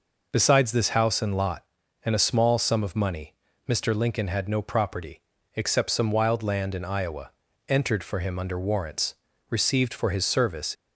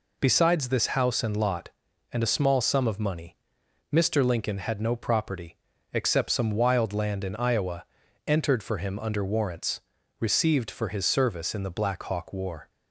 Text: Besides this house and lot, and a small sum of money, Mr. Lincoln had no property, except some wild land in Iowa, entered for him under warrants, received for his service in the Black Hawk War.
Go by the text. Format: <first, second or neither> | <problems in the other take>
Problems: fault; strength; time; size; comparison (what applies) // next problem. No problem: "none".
second | stops before "in the Black Hawk War"; at 10.7 s